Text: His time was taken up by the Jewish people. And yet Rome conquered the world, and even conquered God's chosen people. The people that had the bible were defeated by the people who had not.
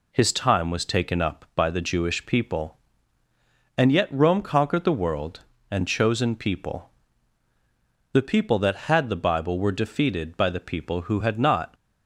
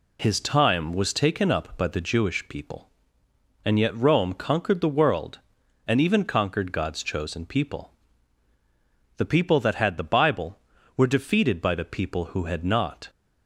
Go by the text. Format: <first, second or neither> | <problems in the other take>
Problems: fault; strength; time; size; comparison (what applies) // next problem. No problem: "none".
second | skips "even conquered God's"; at 5.8 s